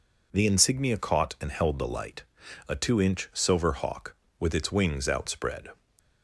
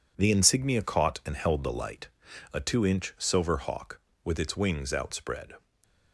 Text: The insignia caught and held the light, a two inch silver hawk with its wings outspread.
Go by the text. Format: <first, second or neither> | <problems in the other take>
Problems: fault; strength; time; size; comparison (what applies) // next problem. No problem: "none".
first | gets quieter; strong; throughout; 8.5 dB // stays silent after the last word; slight; from 5.5 s on; 0.6 s long